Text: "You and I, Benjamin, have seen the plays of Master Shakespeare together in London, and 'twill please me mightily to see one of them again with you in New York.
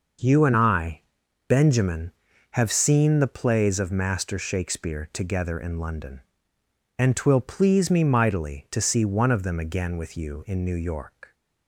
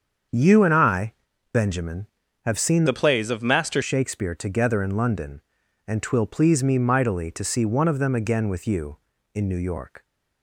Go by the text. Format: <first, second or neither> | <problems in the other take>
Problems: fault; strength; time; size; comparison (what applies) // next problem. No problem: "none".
first | starts louder than the rest; strong; until 1.6 s; 7 dB // changes voice from "the" to "Master"; from 2.8 to 3.8 s; 1.0 s long